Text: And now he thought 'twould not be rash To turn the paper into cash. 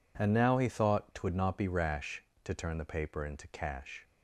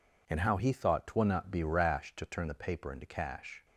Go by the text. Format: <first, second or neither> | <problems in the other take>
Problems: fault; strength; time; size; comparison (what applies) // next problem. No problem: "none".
first | says "how" for "now"; at 0.3 s